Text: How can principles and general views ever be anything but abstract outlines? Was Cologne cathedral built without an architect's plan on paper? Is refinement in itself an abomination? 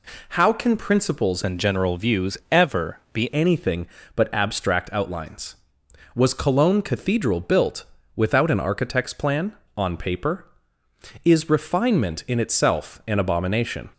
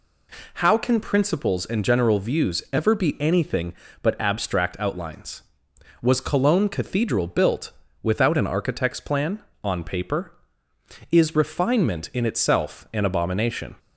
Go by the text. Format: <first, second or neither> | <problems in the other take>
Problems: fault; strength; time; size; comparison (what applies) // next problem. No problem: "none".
second | changes voice from "and" to "be"; from 1.4 to 3.3 s; 1.9 s long // pauses between "built" and "without"; slight; at 7.8 s; 0.30 s long; slight in the second